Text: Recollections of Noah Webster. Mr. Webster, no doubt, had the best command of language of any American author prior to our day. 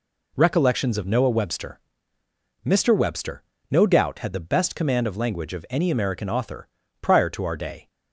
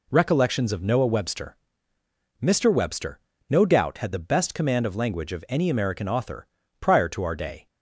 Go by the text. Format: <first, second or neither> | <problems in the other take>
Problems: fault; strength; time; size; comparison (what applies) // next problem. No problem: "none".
neither | pauses between "author" and "prior"; slight; the same in both